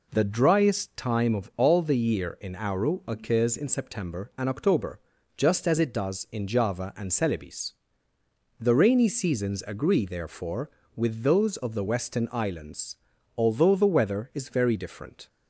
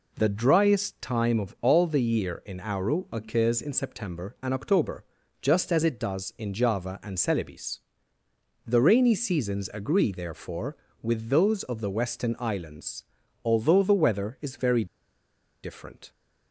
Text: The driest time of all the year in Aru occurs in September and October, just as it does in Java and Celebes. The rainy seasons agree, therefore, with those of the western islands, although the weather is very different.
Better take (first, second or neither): first